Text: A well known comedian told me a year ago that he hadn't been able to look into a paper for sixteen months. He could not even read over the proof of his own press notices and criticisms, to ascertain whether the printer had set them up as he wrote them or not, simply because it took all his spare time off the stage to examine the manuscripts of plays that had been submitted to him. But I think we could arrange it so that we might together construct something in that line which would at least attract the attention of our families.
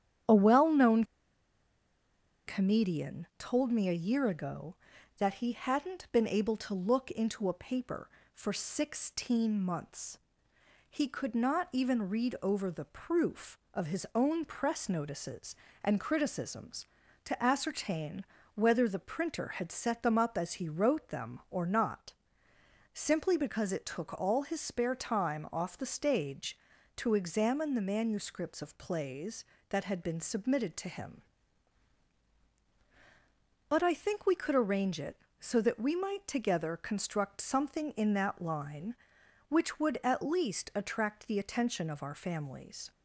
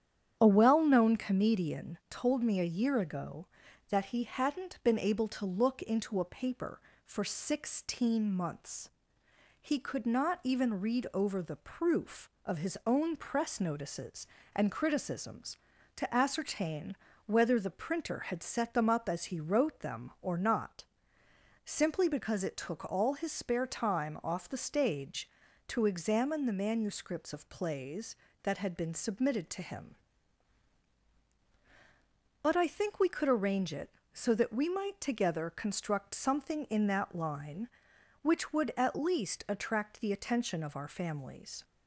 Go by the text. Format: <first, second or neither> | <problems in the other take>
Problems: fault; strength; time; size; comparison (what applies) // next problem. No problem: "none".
second | starts louder than the rest; strong; until 2.7 s; 9.5 dB; strong in the second // pauses between "known" and "comedian"; strong; at 1.0 s; 1.4 s long // pauses between "ascertain" and "whether"; slight; at 18.2 s; 0.30 s long; slight in the second